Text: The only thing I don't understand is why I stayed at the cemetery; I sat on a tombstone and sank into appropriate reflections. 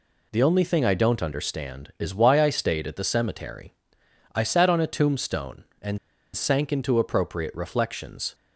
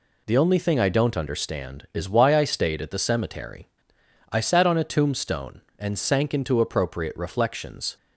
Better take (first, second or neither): second